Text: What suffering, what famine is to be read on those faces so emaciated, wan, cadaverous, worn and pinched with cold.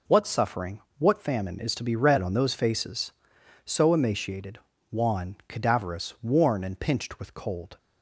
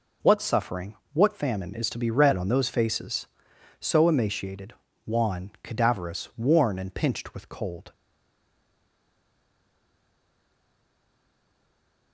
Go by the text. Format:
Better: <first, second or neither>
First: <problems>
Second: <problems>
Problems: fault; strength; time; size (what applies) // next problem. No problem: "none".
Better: first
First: none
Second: stays silent after the last word; strong; from 7.9 s on; 4.2 s long